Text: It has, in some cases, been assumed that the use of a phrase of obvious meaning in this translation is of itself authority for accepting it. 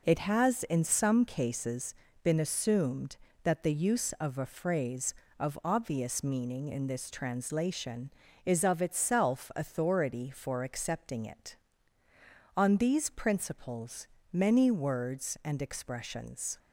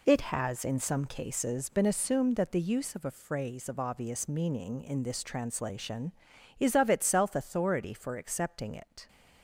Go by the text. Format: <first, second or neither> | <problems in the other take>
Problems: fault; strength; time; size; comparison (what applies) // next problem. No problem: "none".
second | goes on to say "On these principles many words and expressions"; strong; from 12.5 s on; 4.0 s long